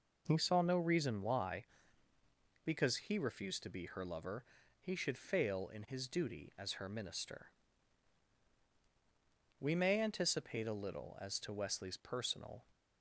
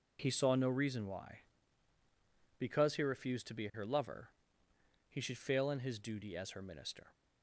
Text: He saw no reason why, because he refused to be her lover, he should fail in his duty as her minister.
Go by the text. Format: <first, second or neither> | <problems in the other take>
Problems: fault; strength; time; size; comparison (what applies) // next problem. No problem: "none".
second | goes on to say "We may anticipate a little as to Wesley's personal"; strong; from 9.5 s on; 3.1 s long